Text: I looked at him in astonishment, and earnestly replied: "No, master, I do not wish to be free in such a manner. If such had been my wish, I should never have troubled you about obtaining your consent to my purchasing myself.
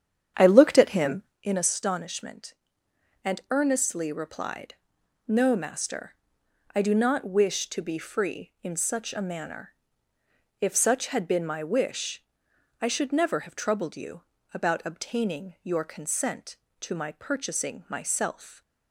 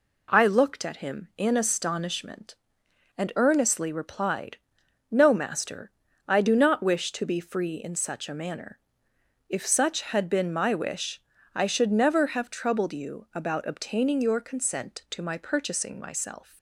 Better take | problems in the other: second | starts louder than the rest; strong; until 1.4 s; 9 dB // pauses between "you" and "about"; slight; at 14.2 s; 0.32 s long

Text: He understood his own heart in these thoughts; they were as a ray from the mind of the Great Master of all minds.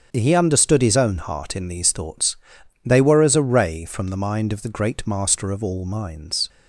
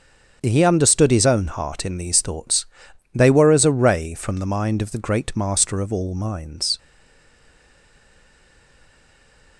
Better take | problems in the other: first | starts louder than the rest; strong; until 1.4 s; 7.5 dB; strong in the first // stays silent after the last word; strong; from 6.7 s on; 2.8 s long

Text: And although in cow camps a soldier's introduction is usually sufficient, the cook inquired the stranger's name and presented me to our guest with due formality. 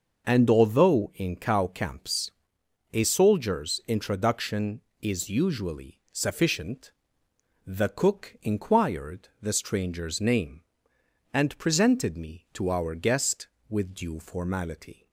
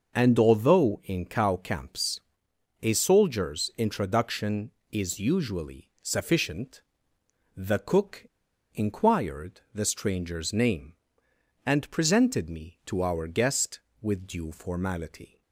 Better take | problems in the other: first | starts louder than the rest; noticeable; until 1.1 s; 6 dB // pauses between "camps" and "a"; noticeable; at 2.1 s; 0.62 s long; noticeable in the first // pauses between "cook" and "inquired"; noticeable; at 8.2 s; 0.48 s long

